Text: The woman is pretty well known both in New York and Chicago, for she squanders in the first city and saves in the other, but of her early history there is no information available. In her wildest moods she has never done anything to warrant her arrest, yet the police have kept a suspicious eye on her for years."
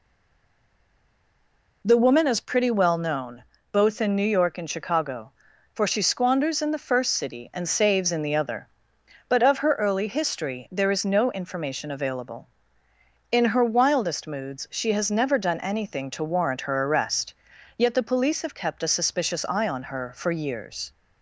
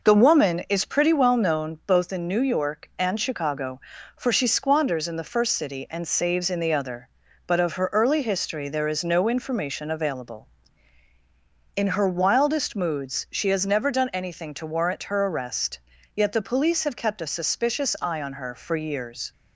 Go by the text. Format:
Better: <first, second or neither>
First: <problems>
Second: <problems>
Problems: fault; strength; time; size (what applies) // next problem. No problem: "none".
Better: second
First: stays silent before the first word; noticeable; until 1.8 s; 1.8 s long // pauses between "known" and "both"; slight; at 3.4 s; 0.28 s long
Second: none